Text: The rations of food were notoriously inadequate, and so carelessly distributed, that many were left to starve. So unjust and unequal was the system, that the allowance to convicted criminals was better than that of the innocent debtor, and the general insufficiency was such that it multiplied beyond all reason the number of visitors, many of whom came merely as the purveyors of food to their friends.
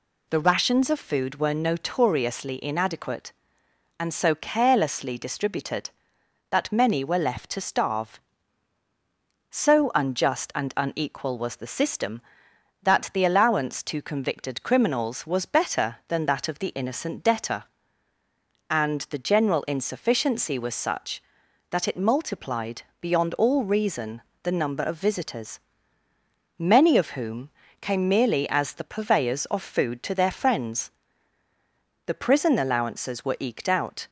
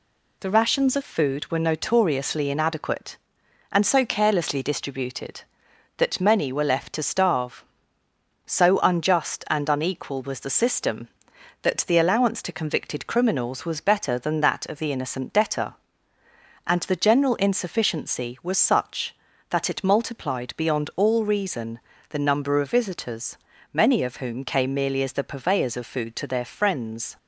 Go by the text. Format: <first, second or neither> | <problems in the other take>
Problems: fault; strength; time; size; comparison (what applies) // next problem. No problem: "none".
second | pauses between "multiplied" and "beyond"; slight; at 22.8 s; 0.18 s long // pauses between "reason" and "the"; slight; at 24.2 s; 0.22 s long; slight in the second // pauses between "whom" and "came"; slight; at 27.4 s; 0.32 s long // goes on to say "The prison allowances were eked out"; strong; from 32.0 s on; 2.0 s long